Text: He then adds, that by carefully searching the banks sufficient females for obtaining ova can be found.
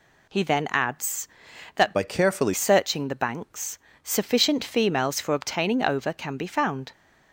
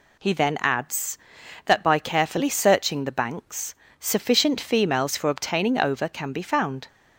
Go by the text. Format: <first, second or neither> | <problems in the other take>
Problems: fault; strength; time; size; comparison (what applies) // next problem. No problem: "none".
second | changes voice from "by" to "carefully"; from 1.9 to 2.5 s; 0.6 s long // pauses between "banks" and "sufficient"; slight; at 3.7 s; 0.26 s long; slight in the second